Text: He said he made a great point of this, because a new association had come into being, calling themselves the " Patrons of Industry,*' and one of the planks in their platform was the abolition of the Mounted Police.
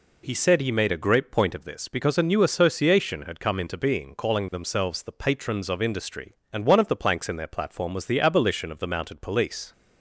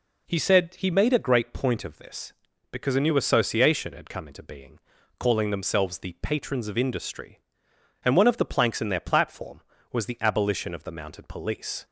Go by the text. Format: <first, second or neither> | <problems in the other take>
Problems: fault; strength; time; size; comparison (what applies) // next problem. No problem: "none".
neither | none